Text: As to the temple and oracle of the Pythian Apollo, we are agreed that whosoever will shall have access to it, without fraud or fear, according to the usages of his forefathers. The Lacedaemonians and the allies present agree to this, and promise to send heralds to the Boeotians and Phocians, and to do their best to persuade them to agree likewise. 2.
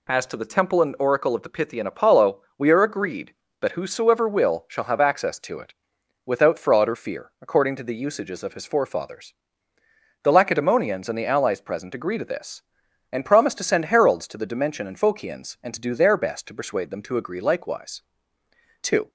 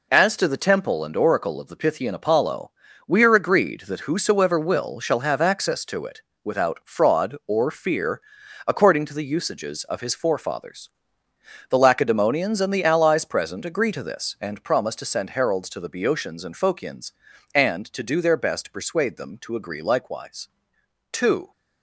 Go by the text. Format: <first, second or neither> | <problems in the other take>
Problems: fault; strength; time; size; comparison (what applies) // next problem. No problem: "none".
second | says "Dimension" for "Boeotians"; at 14.4 s